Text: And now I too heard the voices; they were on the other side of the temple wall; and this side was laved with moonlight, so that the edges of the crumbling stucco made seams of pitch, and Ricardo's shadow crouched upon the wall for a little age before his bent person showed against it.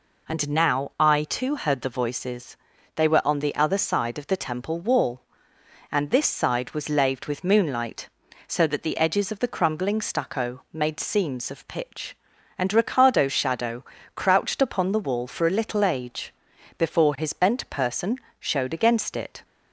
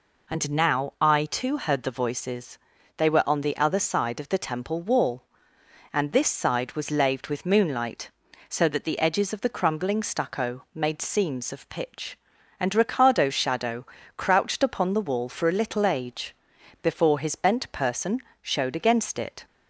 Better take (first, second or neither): neither